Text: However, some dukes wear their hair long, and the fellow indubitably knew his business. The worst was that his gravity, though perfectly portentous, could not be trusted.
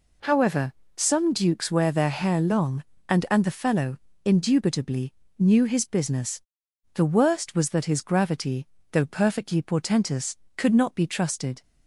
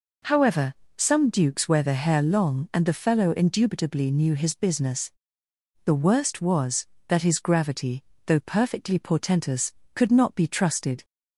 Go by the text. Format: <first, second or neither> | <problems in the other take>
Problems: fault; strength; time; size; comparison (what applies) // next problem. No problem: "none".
second | says "and" twice; at 3.2 s // pauses between "fellow" and "indubitably"; slight; at 3.9 s; 0.26 s long // pauses between "indubitably" and "knew"; slight; at 5.1 s; 0.26 s long